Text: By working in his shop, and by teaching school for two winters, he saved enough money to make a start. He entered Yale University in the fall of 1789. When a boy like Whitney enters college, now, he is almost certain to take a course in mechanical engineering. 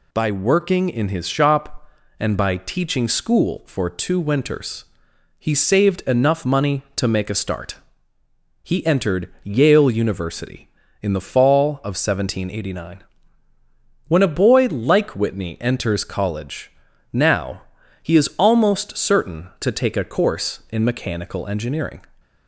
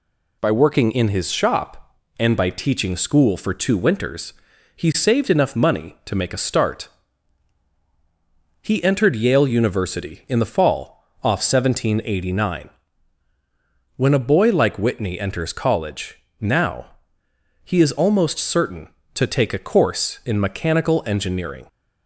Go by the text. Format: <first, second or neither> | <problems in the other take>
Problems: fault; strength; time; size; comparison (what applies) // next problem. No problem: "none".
first | says "off" for "of"; at 11.2 s